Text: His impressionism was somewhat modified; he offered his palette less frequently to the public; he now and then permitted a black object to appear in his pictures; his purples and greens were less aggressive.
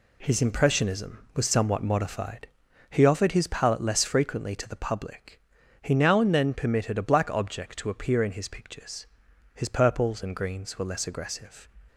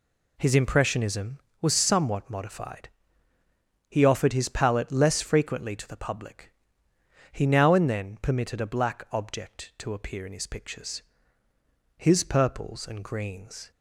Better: first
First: none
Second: stops before "were less aggressive"; at 13.7 s

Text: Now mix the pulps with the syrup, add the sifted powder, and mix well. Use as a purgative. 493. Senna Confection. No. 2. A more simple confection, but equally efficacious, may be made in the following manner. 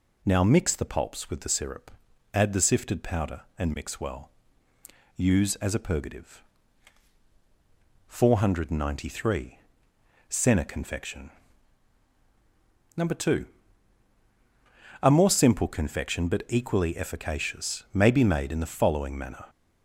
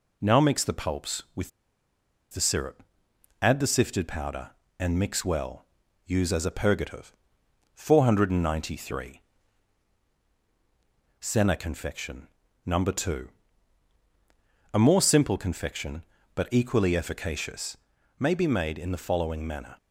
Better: first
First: none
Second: pauses between "with" and "the"; noticeable; at 1.5 s; 0.82 s long

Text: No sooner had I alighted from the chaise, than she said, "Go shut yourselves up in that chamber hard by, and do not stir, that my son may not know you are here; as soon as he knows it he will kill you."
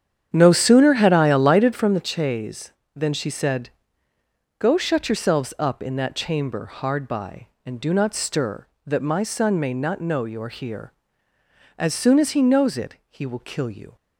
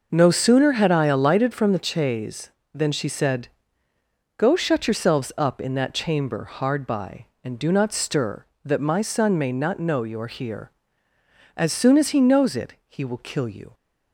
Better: second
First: starts louder than the rest; strong; until 1.9 s; 9 dB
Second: none

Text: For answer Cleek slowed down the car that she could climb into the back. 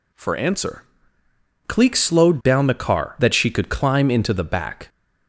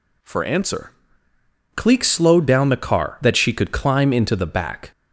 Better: neither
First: pauses between "answer" and "Cleek"; noticeable; at 0.8 s; 0.84 s long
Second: pauses between "answer" and "Cleek"; noticeable; at 0.9 s; 0.84 s long

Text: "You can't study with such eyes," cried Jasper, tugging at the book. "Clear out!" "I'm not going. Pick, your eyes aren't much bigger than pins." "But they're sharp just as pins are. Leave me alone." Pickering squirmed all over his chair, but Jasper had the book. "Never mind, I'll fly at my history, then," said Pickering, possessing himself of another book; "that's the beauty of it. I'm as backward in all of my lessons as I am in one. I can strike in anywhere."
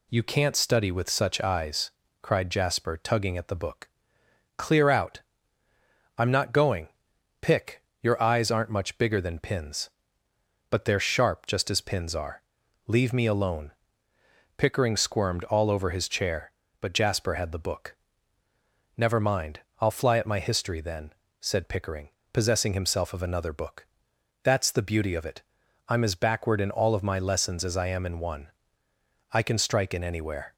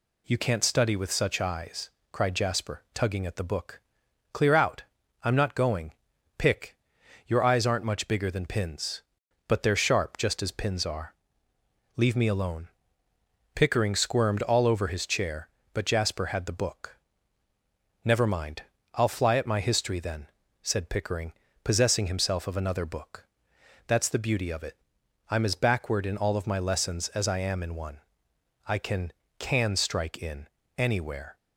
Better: first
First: none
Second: says "can" twice; at 29.3 s // pauses between "in" and "anywhere"; slight; at 30.4 s; 0.32 s long

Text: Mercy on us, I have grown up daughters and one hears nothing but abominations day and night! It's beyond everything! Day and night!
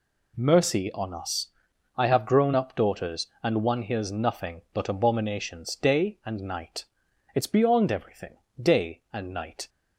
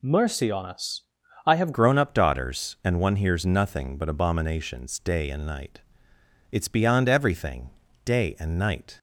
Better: first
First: none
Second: changes voice at "grown"; from 1.7 s on; 7.2 s long

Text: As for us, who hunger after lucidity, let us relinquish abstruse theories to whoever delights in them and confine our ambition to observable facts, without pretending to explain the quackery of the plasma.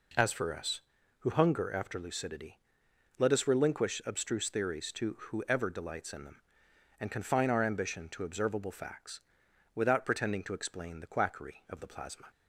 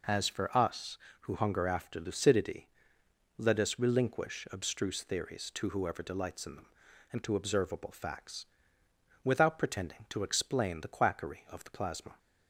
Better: first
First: none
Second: skips "confine our ambition"; at 7.2 s

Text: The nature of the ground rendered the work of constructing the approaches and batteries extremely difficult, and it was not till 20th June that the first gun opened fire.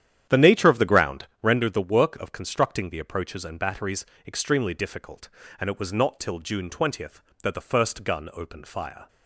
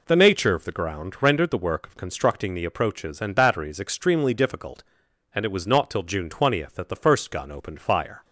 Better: second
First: starts louder than the rest; strong; until 1.7 s; 10 dB // pauses between "ground" and "rendered"; slight; at 1.2 s; 0.16 s long // pauses between "batteries" and "extremely"; slight; at 4.0 s; 0.22 s long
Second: none

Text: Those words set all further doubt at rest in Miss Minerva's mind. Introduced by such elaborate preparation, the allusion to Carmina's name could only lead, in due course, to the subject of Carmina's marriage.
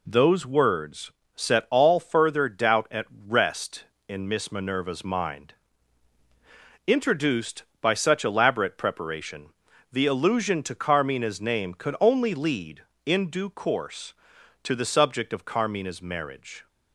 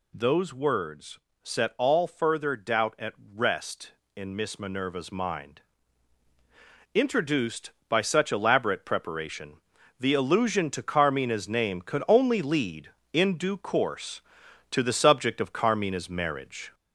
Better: first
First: pauses between "words" and "set"; slight; at 1.1 s; 0.24 s long // pauses between "at" and "rest"; slight; at 3.0 s; 0.20 s long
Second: gets louder; slight; throughout; 3 dB // pauses between "words" and "set"; slight; at 1.1 s; 0.24 s long // pauses between "at" and "rest"; slight; at 3.1 s; 0.20 s long

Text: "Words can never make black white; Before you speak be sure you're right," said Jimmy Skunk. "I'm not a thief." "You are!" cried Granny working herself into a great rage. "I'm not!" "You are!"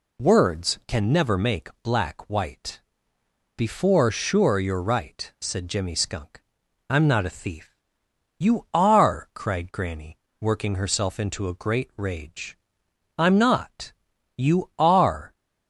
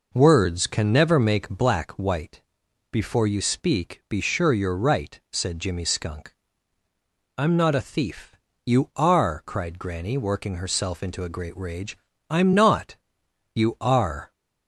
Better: second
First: pauses between "make" and "black"; slight; at 1.6 s; 0.16 s long // skips "you speak be"; at 4.0 s // pauses between "Granny" and "working"; slight; at 10.1 s; 0.22 s long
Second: none

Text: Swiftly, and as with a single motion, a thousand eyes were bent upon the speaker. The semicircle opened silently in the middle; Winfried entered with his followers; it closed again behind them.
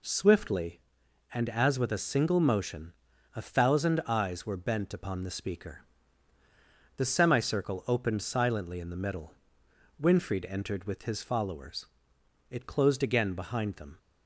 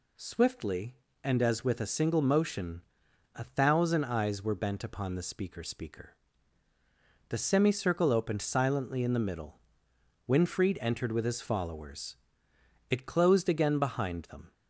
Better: first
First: none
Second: says "speaker" twice; at 5.6 s

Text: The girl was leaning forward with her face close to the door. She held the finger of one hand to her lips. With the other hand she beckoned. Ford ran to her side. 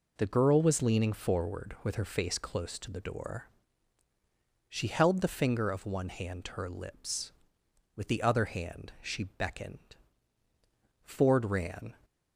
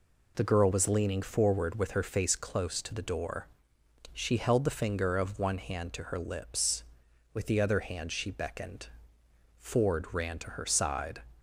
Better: second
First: stops before "to her side"; at 12.0 s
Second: none

